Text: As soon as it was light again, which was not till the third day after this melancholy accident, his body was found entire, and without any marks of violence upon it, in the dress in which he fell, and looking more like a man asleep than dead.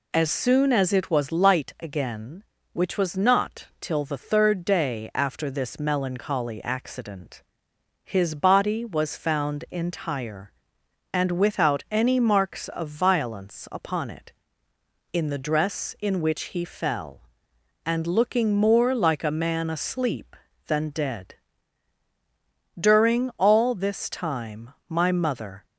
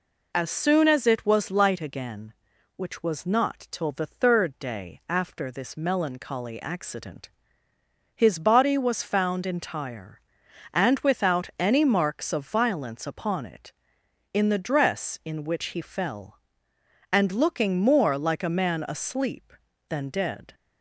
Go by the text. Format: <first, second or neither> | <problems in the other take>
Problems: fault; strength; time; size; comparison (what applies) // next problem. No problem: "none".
second | goes on to say "During all this time my mother"; strong; from 22.7 s on; 2.8 s long